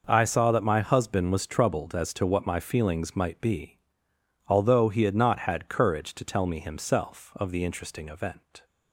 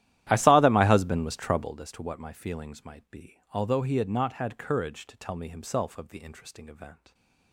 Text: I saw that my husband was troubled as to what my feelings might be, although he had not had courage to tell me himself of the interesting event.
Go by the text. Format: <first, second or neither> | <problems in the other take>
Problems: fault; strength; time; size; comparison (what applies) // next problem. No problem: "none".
first | starts louder than the rest; strong; until 1.9 s; 13 dB